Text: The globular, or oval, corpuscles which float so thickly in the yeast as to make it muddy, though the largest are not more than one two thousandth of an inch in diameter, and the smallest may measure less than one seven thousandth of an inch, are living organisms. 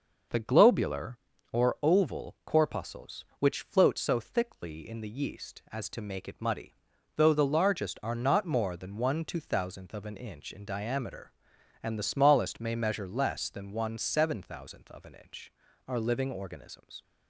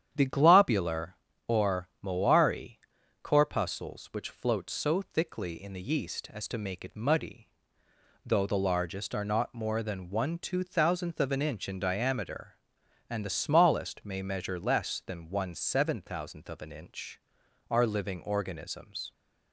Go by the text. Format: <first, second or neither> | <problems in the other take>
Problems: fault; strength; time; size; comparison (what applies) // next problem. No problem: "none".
first | starts louder than the rest; strong; until 1.1 s; 9.5 dB; noticeable in the first // says "moari" for "oval"; at 2.0 s